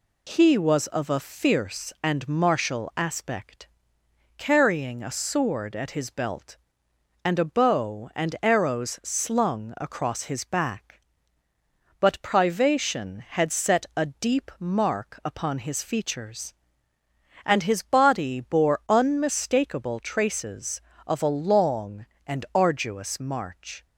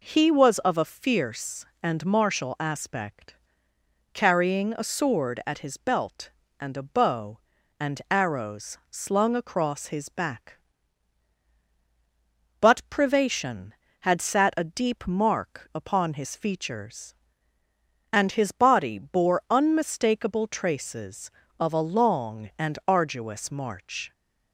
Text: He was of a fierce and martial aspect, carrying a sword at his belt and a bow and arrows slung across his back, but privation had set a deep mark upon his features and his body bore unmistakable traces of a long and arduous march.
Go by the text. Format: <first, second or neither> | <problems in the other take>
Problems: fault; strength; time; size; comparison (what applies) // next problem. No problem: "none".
first | says "sat" for "set"; at 14.1 s